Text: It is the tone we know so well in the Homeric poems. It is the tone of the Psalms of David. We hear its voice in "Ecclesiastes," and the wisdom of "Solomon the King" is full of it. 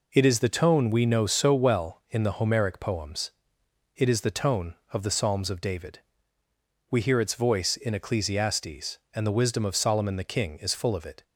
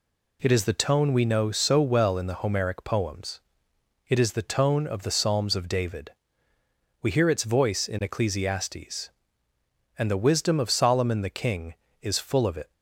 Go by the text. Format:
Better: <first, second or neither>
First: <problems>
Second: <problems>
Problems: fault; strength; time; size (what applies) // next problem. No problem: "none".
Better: neither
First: none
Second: none